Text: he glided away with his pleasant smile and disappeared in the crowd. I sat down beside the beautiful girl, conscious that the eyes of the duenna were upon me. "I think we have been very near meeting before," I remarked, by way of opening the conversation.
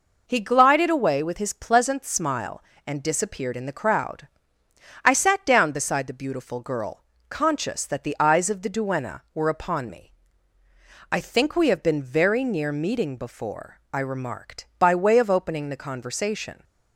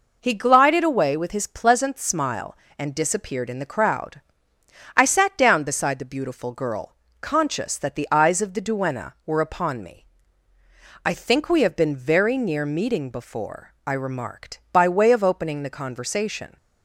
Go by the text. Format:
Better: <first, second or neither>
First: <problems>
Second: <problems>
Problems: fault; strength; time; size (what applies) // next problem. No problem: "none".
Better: neither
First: none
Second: none